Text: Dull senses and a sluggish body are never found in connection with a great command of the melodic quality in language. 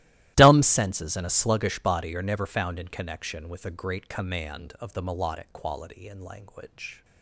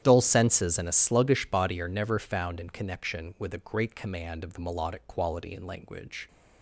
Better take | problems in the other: second | starts louder than the rest; strong; until 1.3 s; 15.5 dB; strong in the second // says "Dumb" for "Dull"; at 0.3 s

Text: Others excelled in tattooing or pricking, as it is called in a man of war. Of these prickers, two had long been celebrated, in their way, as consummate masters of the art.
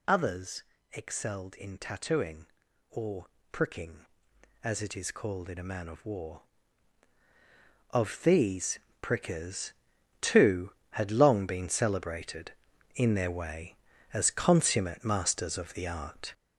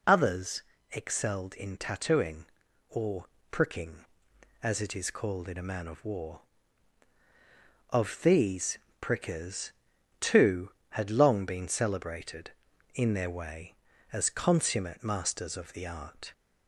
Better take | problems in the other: second | gets louder; throughout; 6.5 dB // pauses between "Others" and "excelled"; slight; at 0.6 s; 0.28 s long; slight in the second // pauses between "or" and "pricking"; slight; at 3.2 s; 0.24 s long; slight in the second // pauses between "these" and "prickers"; slight; at 8.7 s; 0.22 s long; slight in the second

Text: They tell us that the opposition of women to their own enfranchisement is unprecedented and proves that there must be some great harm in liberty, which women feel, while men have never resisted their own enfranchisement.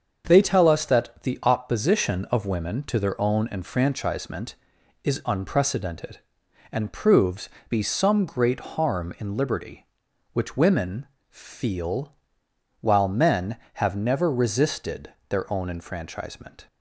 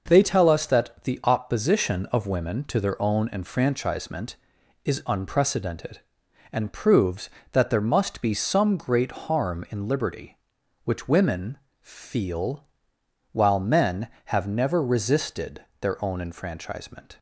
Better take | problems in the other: second | starts louder than the rest; until 1.2 s; 6.5 dB // skips "that there must"; at 7.5 s // pauses between "women" and "feel"; slight; at 11.0 s; 0.22 s long; slight in the second // pauses between "resisted" and "their"; slight; at 15.1 s; 0.16 s long; slight in the second

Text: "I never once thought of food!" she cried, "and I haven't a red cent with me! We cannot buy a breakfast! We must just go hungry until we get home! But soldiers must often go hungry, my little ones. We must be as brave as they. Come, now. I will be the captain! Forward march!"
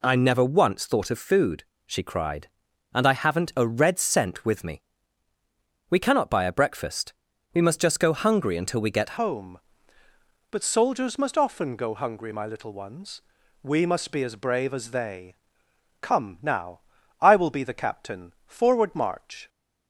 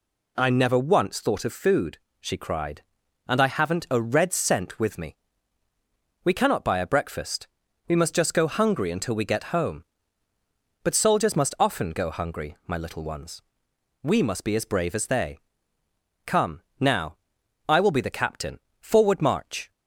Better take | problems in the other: second | changes voice at "home"; from 9.1 s on; 10.3 s long

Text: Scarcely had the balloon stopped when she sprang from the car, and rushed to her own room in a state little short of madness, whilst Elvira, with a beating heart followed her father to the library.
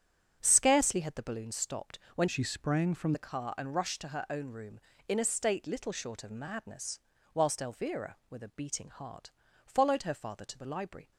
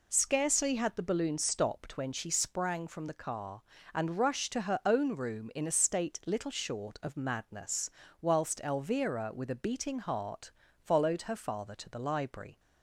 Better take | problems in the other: second | starts louder than the rest; strong; until 1.4 s; 8.5 dB // pauses between "stopped" and "when"; slight; at 1.9 s; 0.18 s long // changes voice from "she" to "from"; from 2.2 to 3.1 s; 0.9 s long // pauses between "heart" and "followed"; slight; at 9.3 s; 0.34 s long; slight in the second

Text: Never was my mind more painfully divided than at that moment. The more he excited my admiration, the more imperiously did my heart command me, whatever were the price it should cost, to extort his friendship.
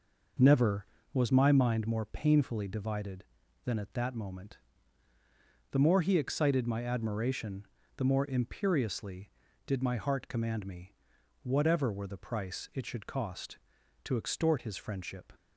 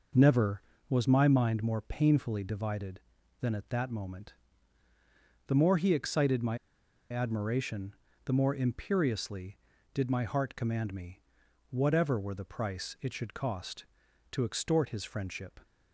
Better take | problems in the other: first | pauses between "my" and "admiration"; noticeable; at 6.5 s; 0.54 s long

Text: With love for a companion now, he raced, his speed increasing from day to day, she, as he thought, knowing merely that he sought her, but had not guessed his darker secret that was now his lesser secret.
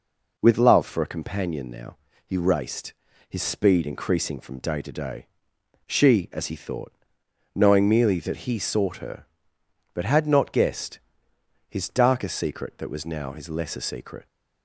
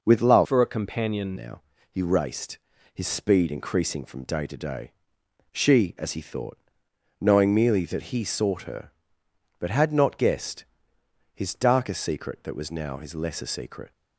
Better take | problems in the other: first | changes voice from "for" to "companion"; from 0.4 to 1.3 s; 0.9 s long // pauses between "guessed" and "his"; noticeable; at 10.6 s; 0.70 s long; noticeable in the first

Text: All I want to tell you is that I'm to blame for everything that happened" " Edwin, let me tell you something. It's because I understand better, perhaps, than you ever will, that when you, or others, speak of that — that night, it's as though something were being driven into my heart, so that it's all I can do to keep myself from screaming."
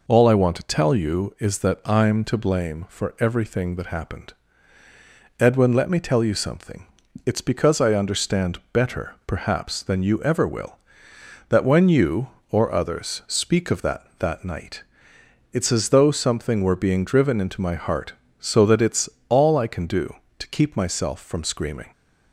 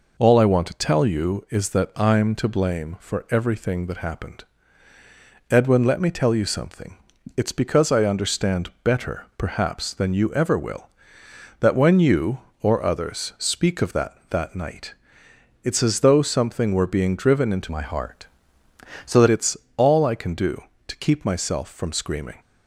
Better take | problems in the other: first | changes voice from "my" to "that"; from 17.7 to 19.2 s; 1.5 s long // pauses between "it's" and "all"; slight; at 19.5 s; 0.22 s long; slight in the first

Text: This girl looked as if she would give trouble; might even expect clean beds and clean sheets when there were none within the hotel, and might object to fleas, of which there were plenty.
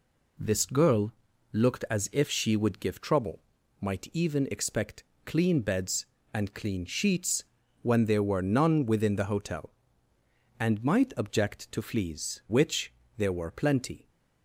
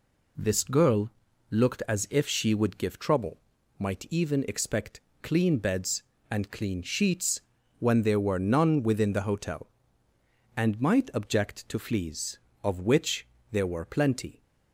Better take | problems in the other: second | pauses between "girl" and "looked"; at 1.1 s; 0.40 s long; also in the second // pauses between "expect" and "clean"; slight; at 5.0 s; 0.22 s long; slight in the second // pauses between "sheets" and "when"; at 7.4 s; 0.40 s long; also in the second // skips "of"; at 12.4 s // pauses between "which" and "there"; slight; at 12.9 s; 0.26 s long; slight in the second

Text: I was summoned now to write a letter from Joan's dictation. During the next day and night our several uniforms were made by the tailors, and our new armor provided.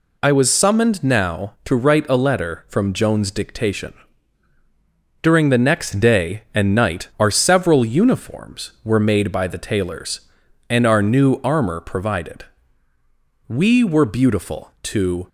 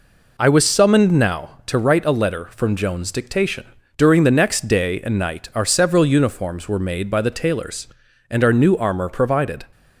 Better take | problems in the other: second | goes on to say "We were beautiful to"; strong; from 13.4 s on; 1.8 s long

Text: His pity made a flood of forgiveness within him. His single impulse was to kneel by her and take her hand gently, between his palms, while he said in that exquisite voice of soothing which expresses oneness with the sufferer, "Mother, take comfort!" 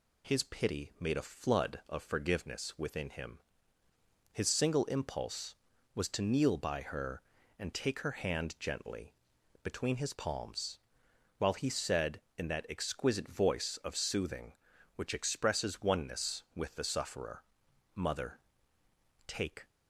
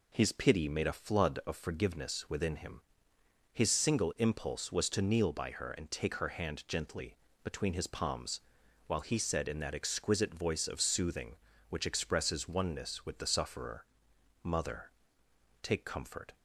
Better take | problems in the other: second | stops before "comfort"; at 19.6 s

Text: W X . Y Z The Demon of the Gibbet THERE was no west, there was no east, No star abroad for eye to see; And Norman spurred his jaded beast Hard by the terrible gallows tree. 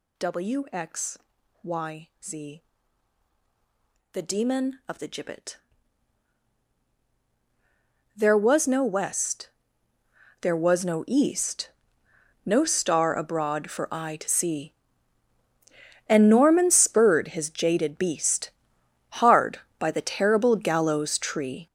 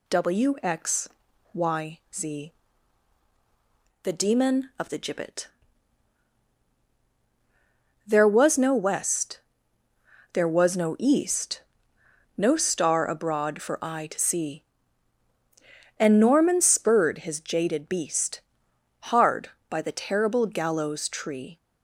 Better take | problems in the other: second | gets louder; strong; throughout; 10 dB // pauses between "Y" and "Z"; slight; at 2.0 s; 0.16 s long; slight in the second // pauses between "Z" and "The"; strong; at 2.6 s; 1.5 s long; strong in the second // pauses between "Gibbet" and "THERE"; strong; at 5.5 s; 2.5 s long; strong in the second // pauses between "beast" and "Hard"; noticeable; at 18.5 s; 0.64 s long; noticeable in the second

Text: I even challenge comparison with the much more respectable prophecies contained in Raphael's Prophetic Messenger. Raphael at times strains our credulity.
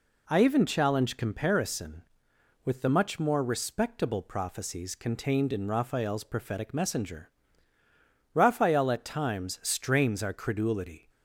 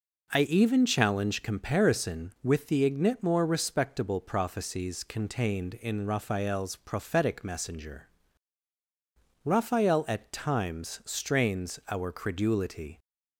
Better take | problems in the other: first | says "ignit" for "much"; at 2.8 s

